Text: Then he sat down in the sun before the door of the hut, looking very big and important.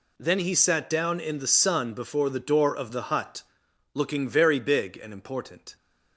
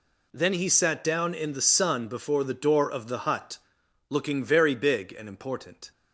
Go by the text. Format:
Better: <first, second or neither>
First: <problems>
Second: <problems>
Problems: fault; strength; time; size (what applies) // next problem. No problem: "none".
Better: neither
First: none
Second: none